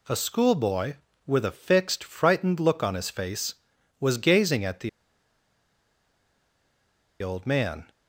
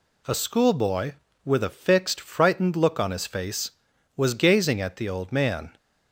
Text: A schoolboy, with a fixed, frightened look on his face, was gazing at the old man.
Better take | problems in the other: second | pauses between "the" and "old"; strong; at 4.8 s; 2.3 s long

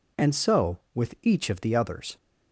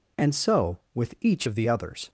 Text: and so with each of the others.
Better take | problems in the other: first | changes voice from "of" to "the"; from 1.4 to 1.6 s; 0.2 s long

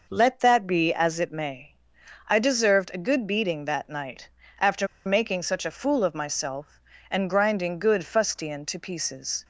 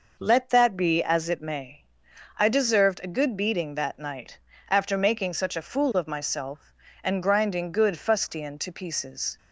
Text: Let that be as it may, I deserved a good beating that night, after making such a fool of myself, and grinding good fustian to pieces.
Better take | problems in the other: second | pauses between "after" and "making"; slight; at 4.8 s; 0.19 s long

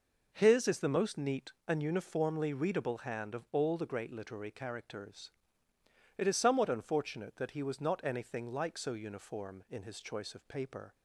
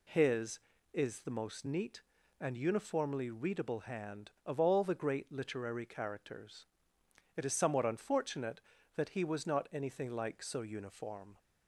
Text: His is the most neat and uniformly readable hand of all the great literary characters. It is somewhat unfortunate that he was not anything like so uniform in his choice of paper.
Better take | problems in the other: first | stops before "in his choice of paper"; at 11.3 s

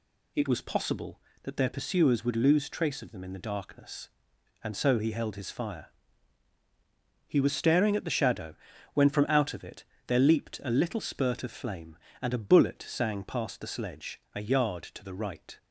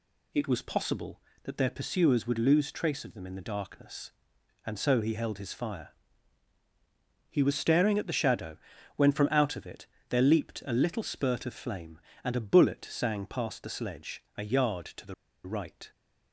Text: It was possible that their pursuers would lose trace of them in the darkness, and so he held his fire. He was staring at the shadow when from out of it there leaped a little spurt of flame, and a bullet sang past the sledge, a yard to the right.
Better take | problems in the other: first | pauses between "shadow" and "when"; at 8.5 s; 0.40 s long; also in the first // pauses between "it" and "there"; slight; at 9.8 s; 0.22 s long; slight in the first // pauses between "the" and "right"; slight; at 15.1 s; 0.32 s long

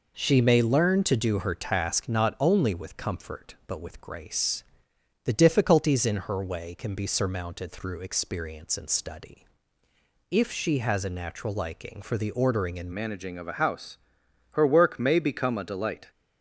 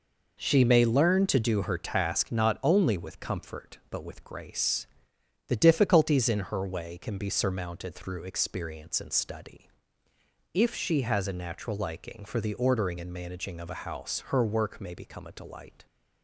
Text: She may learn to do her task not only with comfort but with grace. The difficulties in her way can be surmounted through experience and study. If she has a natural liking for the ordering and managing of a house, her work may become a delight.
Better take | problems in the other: second | changes voice at "managing"; from 12.9 s on; 3.2 s long

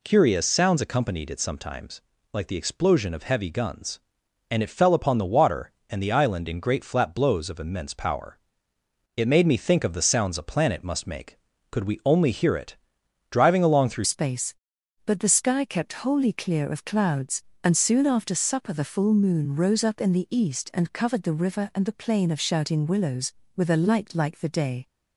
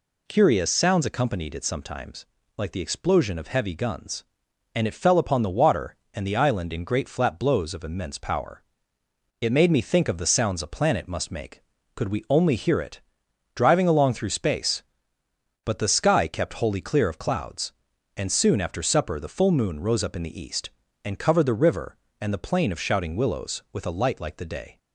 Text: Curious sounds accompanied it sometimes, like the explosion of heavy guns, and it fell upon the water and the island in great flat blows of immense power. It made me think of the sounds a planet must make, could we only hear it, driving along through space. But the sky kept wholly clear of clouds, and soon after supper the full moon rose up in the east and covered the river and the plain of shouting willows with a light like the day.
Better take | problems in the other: second | changes voice at "space"; from 14.0 s on; 10.8 s long

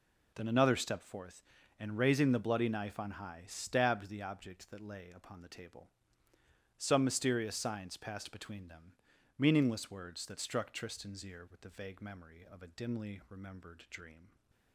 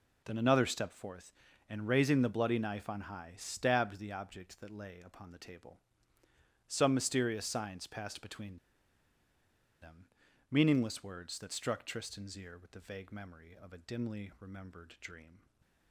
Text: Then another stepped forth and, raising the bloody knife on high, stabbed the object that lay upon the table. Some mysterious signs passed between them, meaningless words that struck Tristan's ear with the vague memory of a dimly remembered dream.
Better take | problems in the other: first | pauses between "between" and "them"; strong; at 8.5 s; 1.2 s long // stays silent after the last word; slight; from 15.3 s on; 0.6 s long

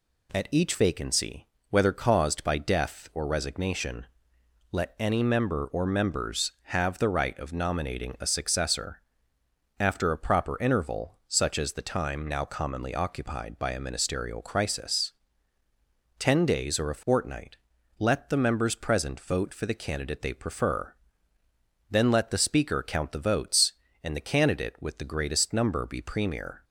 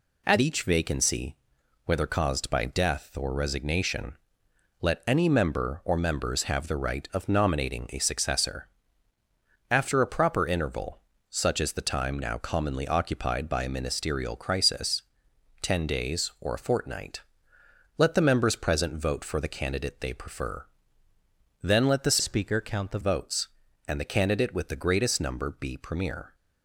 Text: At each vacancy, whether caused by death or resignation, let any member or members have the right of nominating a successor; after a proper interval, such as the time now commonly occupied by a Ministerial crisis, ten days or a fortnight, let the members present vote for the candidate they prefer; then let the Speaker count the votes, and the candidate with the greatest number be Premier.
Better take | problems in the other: first | changes voice from "Speaker" to "the"; from 22.1 to 22.9 s; 0.8 s long

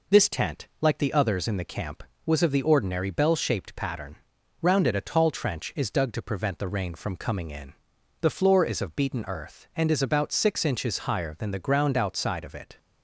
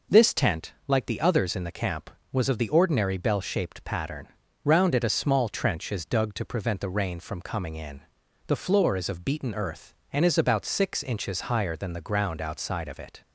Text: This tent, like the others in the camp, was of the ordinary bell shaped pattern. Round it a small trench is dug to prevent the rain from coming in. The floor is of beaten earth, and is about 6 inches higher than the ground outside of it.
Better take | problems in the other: second | says "tall" for "small"; at 5.0 s

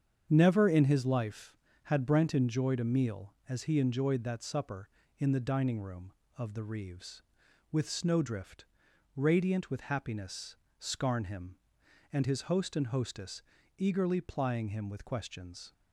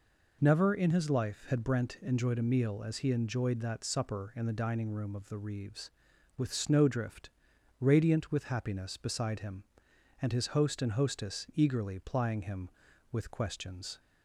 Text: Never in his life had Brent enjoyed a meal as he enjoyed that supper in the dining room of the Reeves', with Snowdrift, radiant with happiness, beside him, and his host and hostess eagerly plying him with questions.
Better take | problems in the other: second | starts louder than the rest; strong; until 1.3 s; 7.5 dB // says "scarn" for "beside"; at 10.7 s // pauses between "hostess" and "eagerly"; at 13.4 s; 0.38 s long

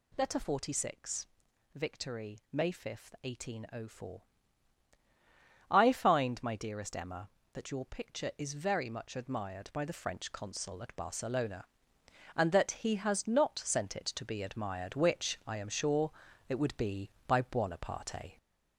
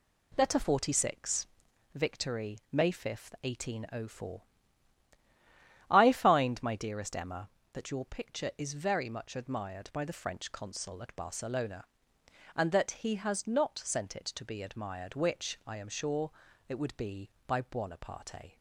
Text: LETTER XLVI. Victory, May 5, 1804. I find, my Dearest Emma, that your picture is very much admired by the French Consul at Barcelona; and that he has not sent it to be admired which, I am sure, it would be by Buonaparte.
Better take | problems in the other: second | gets louder; noticeable; throughout; 4 dB

